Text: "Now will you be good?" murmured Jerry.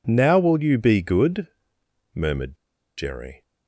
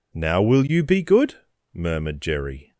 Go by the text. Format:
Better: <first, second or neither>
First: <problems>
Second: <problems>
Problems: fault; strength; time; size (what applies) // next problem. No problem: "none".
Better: second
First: pauses between "murmured" and "Jerry"; at 2.5 s; 0.41 s long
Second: none